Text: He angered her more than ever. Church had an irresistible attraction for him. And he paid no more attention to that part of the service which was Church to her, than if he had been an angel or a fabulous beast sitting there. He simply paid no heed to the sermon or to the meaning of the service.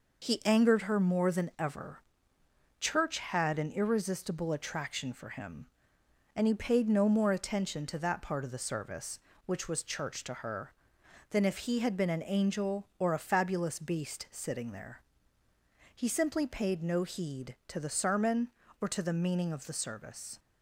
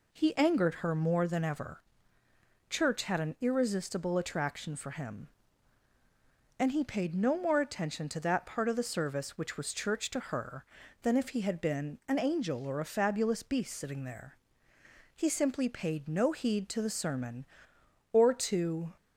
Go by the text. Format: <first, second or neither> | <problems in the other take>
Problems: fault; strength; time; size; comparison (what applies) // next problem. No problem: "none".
first | stops before "the meaning of the service"; at 18.9 s